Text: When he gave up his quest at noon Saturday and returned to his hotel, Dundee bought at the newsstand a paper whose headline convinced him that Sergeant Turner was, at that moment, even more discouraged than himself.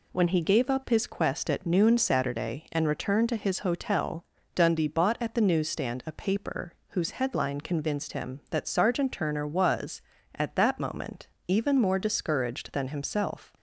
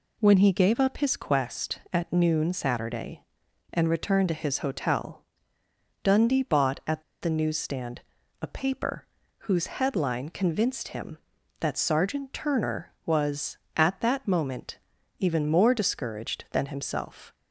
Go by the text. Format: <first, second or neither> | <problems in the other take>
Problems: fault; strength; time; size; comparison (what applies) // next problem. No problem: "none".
first | pauses between "at" and "the"; slight; at 7.0 s; 0.19 s long // pauses between "newsstand" and "a"; at 8.0 s; 0.40 s long // pauses between "paper" and "whose"; slight; at 9.0 s; 0.34 s long; slight in the first